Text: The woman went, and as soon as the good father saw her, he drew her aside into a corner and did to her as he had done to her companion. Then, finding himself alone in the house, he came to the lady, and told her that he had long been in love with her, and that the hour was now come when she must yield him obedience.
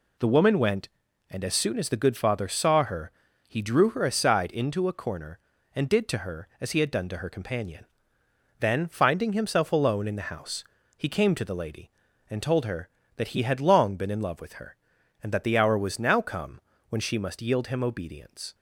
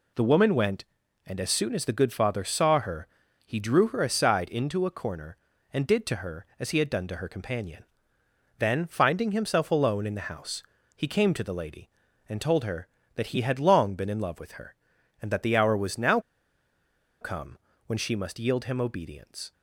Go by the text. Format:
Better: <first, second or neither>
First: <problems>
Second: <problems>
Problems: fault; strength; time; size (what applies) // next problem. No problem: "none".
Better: first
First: pauses between "come" and "when"; slight; at 16.6 s; 0.28 s long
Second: pauses between "now" and "come"; at 16.1 s; 1.0 s long // pauses between "come" and "when"; slight; at 17.5 s; 0.28 s long